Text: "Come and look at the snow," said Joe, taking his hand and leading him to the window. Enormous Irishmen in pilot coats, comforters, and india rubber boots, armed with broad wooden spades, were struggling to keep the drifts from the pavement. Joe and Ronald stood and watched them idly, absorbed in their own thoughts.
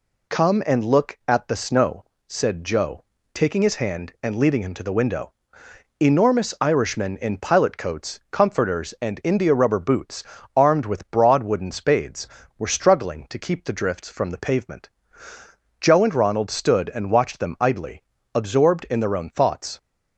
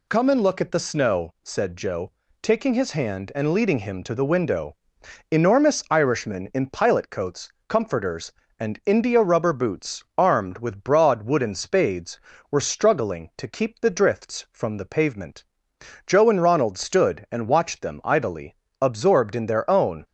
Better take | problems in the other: first | stops before "thoughts"; at 20.0 s

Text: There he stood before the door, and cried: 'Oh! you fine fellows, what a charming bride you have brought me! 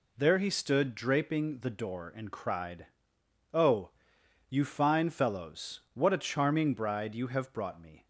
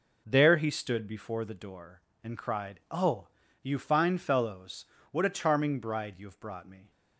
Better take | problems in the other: second | says "draping" for "before"; at 0.9 s

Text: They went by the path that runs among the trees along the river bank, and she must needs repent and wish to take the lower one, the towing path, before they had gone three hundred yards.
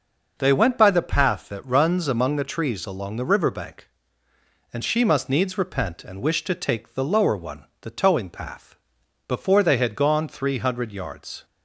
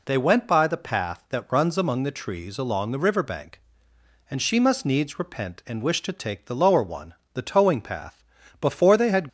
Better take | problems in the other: first | stops before "gone three hundred yards"; at 9.2 s

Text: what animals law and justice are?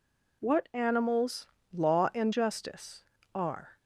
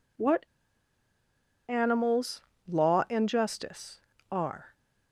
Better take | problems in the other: first | pauses between "what" and "animals"; at 0.4 s; 1.2 s long // pauses between "animals" and "law"; slight; at 2.4 s; 0.26 s long; slight in the first

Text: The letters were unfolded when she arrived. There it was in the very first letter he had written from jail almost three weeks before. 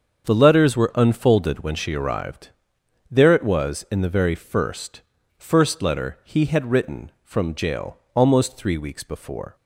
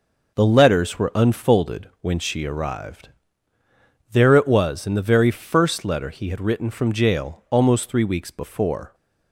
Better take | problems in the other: second | starts louder than the rest; strong; until 1.3 s; 7 dB // says "first" twice; at 5.3 s // pauses between "jail" and "almost"; slight; at 7.9 s; 0.16 s long

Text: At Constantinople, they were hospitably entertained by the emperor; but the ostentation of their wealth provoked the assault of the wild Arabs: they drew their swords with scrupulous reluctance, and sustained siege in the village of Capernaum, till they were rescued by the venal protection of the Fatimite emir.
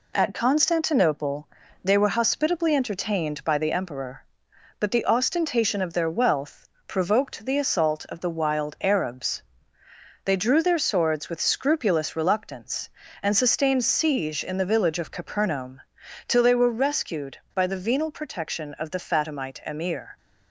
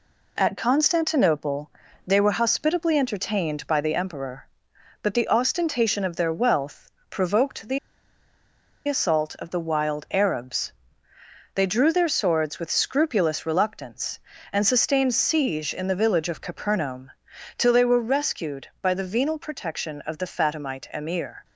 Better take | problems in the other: first | pauses between "wealth" and "provoked"; slight; at 6.9 s; 0.18 s long; slight in the first // pauses between "the" and "assault"; at 7.7 s; 1.0 s long

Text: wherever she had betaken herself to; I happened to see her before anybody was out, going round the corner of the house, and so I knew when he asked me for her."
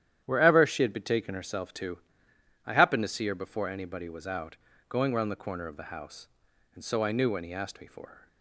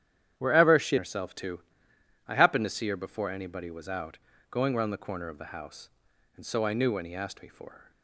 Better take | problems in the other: first | starts louder than the rest; strong; until 1.3 s; 10 dB; strong in the first // skips "had betaken"; at 0.9 s

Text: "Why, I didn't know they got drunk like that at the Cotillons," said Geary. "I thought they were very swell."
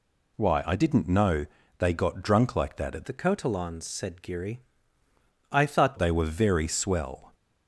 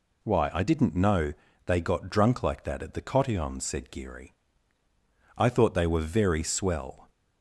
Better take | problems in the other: second | pauses between "know" and "they"; slight; at 1.4 s; 0.32 s long; slight in the second // changes voice from "the" to "thought"; from 3.0 to 5.9 s; 2.9 s long

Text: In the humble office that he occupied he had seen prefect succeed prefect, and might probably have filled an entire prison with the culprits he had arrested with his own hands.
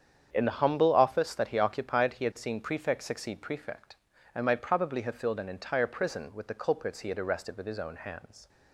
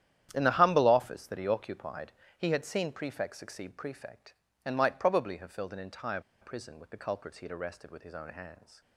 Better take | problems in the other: first | starts louder than the rest; strong; until 1.3 s; 11 dB; strong in the first // pauses between "occupied" and "he"; slight; at 2.1 s; 0.26 s long // pauses between "entire" and "prison"; slight; at 6.1 s; 0.21 s long

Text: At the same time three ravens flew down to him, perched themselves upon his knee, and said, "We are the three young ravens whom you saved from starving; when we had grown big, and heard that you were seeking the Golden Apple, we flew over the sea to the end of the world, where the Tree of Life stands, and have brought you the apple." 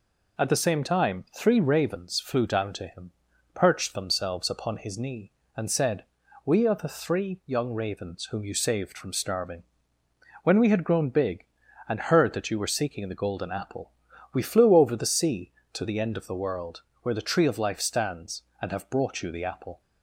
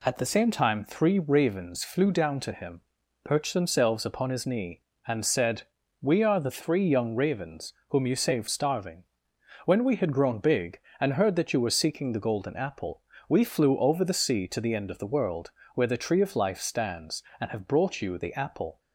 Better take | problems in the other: first | pauses between "ravens" and "whom"; slight; at 7.7 s; 0.18 s long // skips "from"; at 8.4 s

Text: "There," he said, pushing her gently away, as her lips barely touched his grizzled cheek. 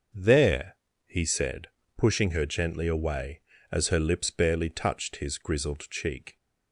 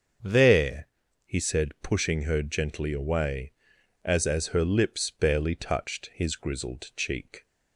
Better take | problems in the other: first | starts louder than the rest; until 1.6 s; 7 dB; also in the first // says "as" twice; at 4.2 s

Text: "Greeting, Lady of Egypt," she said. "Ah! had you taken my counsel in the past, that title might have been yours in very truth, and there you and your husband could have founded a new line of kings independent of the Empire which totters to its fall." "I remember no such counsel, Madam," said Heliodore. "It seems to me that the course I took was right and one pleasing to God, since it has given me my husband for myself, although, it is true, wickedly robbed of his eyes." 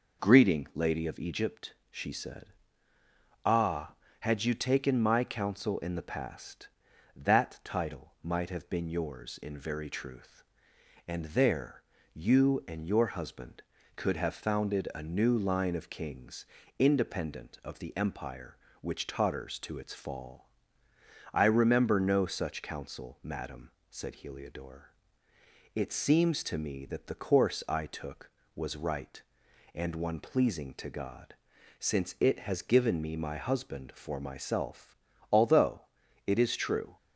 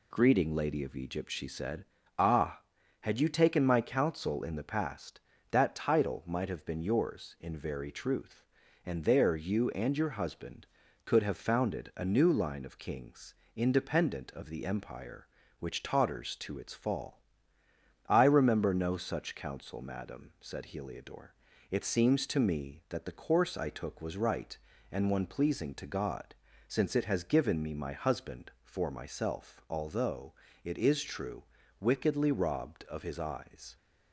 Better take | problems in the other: second | pauses between "there" and "you"; slight; at 11.8 s; 0.30 s long // pauses between "kings" and "independent"; slight; at 16.4 s; 0.34 s long; slight in the second // stops before "wickedly robbed of his eyes"; at 36.9 s

